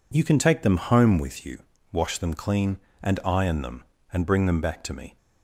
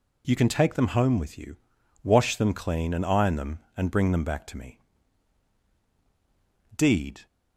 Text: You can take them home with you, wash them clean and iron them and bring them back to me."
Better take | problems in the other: first | goes on to say "Deed"; from 6.7 s on; 0.50 s long

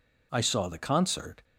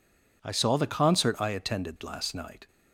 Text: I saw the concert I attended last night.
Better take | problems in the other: second | stops before "I attended last night"; at 1.4 s

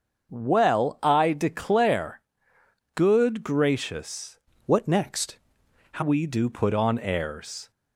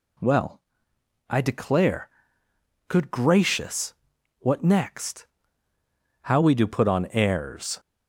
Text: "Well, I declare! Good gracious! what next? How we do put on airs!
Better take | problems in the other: second | starts louder than the rest; until 1.3 s; 7 dB // changes voice from "what" to "How"; from 4.6 to 6.0 s; 1.4 s long

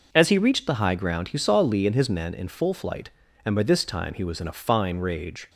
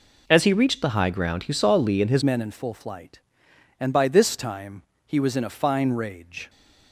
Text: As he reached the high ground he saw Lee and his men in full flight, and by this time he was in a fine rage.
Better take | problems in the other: first | changes voice at "men"; from 2.2 s on; 4.2 s long // pauses between "time" and "he"; slight; at 4.8 s; 0.22 s long

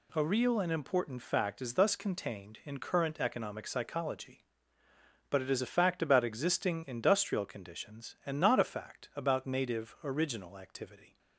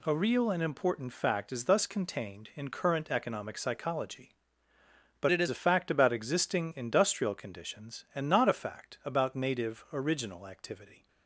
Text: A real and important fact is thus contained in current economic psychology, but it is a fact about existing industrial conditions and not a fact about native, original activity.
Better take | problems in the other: first | changes voice from "it" to "is"; from 5.3 to 5.4 s; 0.1 s long

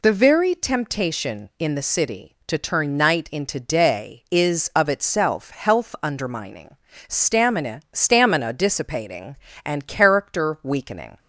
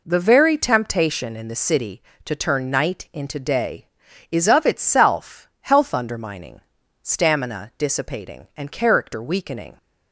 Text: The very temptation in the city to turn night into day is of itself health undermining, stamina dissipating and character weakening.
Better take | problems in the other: second | says "stamina" twice; at 7.9 s

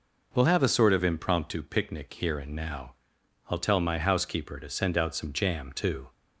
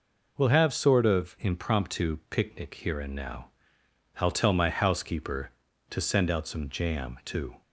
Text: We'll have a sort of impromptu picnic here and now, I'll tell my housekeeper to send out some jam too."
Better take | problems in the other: first | skips "a"; at 0.7 s

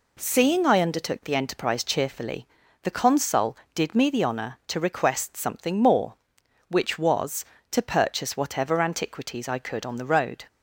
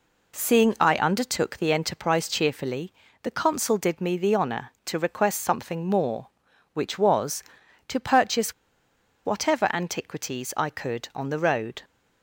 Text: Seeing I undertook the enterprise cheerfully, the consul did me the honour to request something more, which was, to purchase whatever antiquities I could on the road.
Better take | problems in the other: first | pauses between "purchase" and "whatever"; noticeable; at 8.5 s; 0.72 s long

